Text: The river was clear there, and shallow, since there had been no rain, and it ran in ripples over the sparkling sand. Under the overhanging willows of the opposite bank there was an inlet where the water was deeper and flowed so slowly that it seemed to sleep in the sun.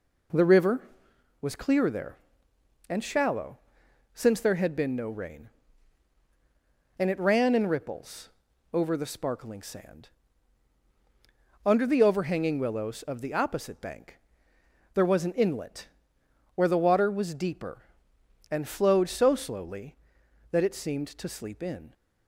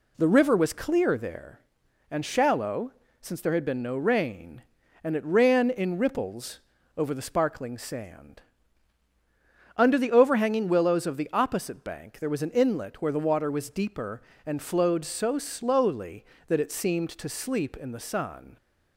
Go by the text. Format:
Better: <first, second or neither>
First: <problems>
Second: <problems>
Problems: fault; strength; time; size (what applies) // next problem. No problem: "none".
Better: second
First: pauses between "ripples" and "over"; at 8.2 s; 0.44 s long // pauses between "bank" and "there"; noticeable; at 14.1 s; 0.74 s long // pauses between "inlet" and "where"; noticeable; at 15.8 s; 0.68 s long // stops before "the sun"; at 21.9 s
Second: pauses between "ripples" and "over"; slight; at 6.6 s; 0.36 s long